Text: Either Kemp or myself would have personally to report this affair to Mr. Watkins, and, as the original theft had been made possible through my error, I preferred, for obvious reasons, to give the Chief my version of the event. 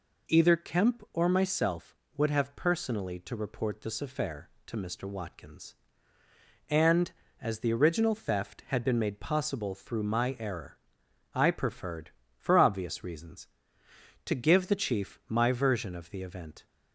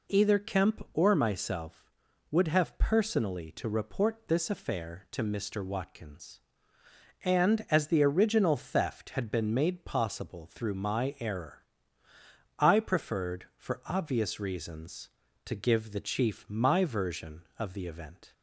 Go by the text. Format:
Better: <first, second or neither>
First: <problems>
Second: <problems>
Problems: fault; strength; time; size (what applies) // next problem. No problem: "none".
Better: neither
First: none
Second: none